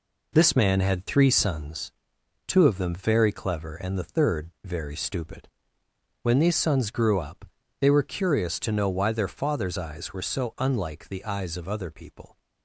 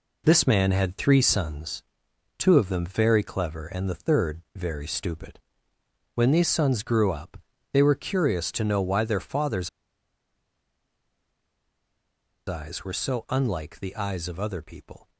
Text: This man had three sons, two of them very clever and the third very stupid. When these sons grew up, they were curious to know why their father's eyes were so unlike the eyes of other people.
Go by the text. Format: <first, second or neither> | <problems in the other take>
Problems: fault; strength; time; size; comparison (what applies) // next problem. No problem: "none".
first | pauses between "father's" and "eyes"; strong; at 9.6 s; 2.7 s long